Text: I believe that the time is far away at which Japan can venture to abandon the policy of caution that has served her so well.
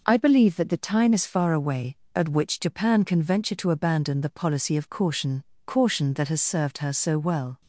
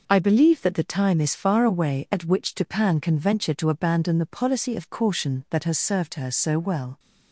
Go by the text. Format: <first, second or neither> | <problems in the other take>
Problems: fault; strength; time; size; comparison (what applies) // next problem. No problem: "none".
second | says "caution" twice; at 5.6 s